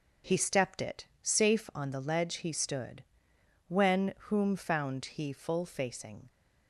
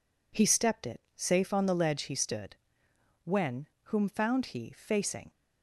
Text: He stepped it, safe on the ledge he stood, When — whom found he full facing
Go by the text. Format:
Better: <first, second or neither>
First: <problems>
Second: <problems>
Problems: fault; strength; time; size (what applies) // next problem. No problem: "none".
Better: first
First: none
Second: skips "full"; at 4.7 s